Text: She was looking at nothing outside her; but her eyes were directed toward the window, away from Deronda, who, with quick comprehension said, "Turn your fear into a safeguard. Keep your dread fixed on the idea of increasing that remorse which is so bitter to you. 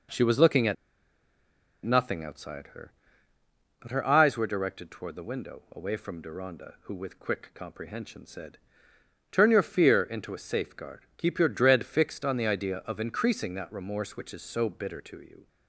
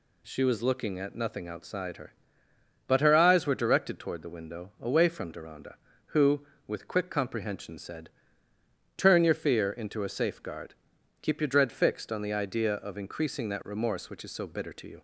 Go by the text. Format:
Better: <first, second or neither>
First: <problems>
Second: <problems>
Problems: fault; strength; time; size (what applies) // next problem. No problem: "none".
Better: second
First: pauses between "at" and "nothing"; at 0.7 s; 1.1 s long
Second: none